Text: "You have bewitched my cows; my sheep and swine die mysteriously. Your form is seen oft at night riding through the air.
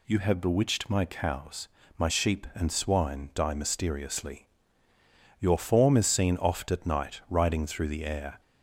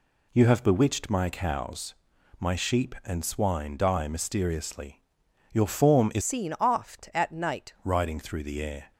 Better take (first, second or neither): first